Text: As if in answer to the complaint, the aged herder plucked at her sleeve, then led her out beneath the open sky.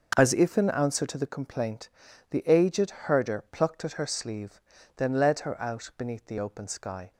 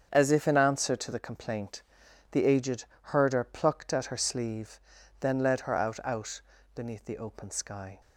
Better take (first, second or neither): first